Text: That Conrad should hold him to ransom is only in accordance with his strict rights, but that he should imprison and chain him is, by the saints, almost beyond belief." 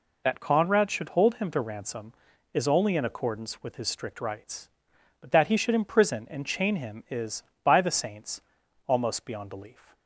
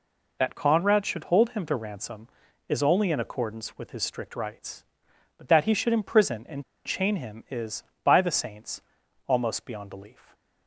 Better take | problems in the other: first | pauses between "and" and "chain"; slight; at 6.6 s; 0.22 s long // stays silent after the last word; slight; from 10.1 s on; 0.5 s long

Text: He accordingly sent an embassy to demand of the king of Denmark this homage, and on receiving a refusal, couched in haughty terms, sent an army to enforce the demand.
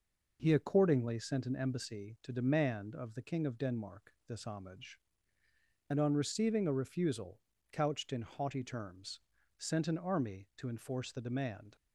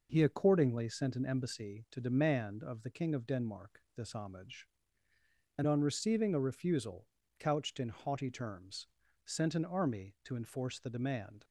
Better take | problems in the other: neither | none

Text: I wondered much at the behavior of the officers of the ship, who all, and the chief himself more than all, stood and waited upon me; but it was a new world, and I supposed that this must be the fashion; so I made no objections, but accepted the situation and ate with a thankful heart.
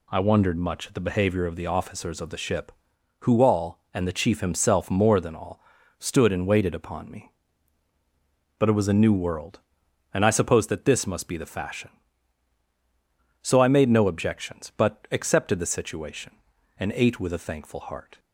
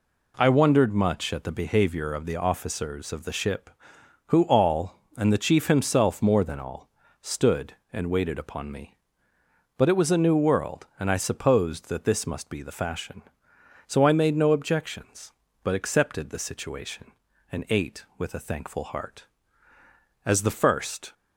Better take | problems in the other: first | goes on to say "As the first"; noticeable; from 20.2 s on; 0.88 s long

